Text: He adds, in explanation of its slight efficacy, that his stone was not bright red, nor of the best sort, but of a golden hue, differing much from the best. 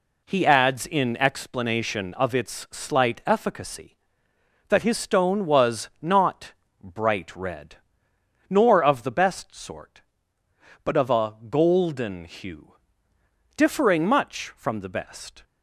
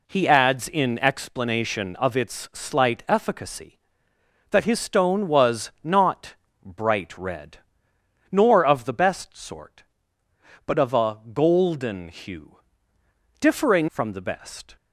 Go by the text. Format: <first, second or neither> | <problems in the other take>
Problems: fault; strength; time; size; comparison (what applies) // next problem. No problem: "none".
first | pauses between "not" and "bright"; slight; at 6.3 s; 0.28 s long; slight in the first // skips "much"; at 13.8 s